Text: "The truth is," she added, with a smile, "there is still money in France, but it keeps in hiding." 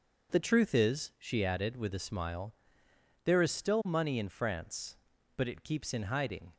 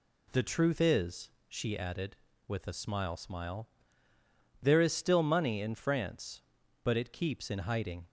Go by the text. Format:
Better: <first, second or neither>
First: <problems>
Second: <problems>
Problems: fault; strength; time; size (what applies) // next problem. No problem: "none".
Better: first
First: none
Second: says "smile" twice; at 3.1 s